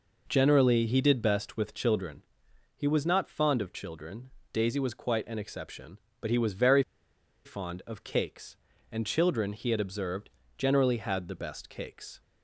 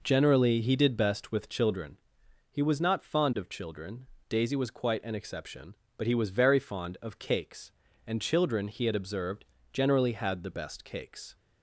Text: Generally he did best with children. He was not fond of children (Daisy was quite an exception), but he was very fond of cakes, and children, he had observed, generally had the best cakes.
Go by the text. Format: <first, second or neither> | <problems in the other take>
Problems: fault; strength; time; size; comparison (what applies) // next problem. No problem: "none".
second | pauses between "very" and "fond"; noticeable; at 6.8 s; 0.62 s long